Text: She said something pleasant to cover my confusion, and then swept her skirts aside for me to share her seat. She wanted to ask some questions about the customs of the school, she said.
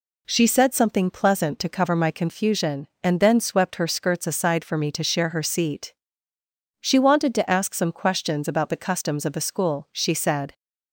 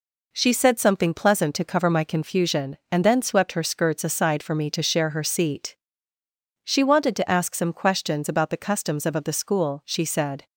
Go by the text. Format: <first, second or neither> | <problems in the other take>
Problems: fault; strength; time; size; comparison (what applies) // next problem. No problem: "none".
first | says "of" twice; at 9.1 s